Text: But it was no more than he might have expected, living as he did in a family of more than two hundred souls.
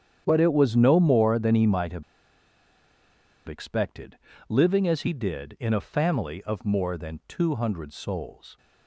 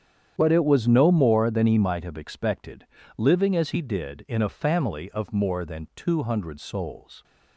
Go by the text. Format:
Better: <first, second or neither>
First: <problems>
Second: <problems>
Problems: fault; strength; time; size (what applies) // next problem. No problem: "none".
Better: second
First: starts louder than the rest; strong; until 1.2 s; 9 dB // pauses between "have" and "expected"; strong; at 2.0 s; 1.4 s long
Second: starts louder than the rest; strong; until 1.3 s; 9 dB